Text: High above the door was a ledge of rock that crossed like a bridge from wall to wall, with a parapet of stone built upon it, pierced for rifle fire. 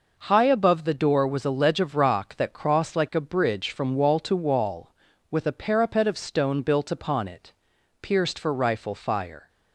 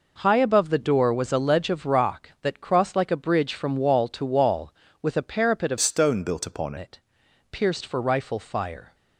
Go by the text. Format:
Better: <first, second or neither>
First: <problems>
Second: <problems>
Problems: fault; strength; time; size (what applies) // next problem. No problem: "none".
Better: first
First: none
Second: changes voice from "stone" to "upon"; from 5.7 to 6.7 s; 1.0 s long